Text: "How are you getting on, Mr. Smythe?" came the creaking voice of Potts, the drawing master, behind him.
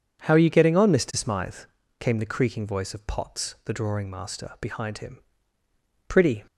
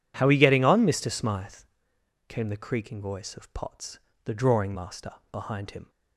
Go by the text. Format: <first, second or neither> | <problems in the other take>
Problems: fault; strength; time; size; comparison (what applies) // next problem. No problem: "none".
second | goes on to say "Pretty"; slight; from 6.0 s on; 0.36 s long